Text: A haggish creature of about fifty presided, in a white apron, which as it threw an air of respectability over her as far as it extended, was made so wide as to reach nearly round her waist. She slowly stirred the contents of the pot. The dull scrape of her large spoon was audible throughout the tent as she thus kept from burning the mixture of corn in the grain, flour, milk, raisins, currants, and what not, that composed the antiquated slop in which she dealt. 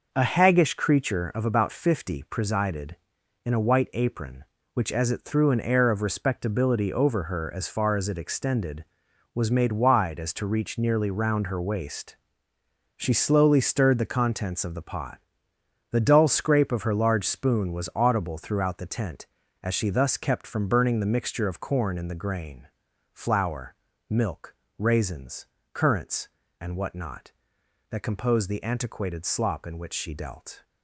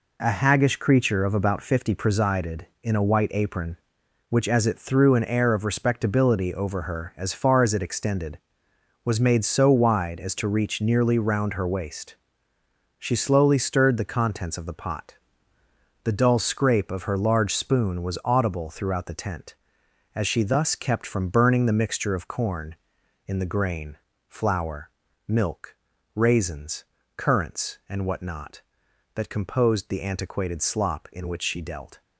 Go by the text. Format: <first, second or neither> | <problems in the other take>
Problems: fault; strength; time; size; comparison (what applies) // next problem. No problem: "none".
second | skips "so"; at 9.7 s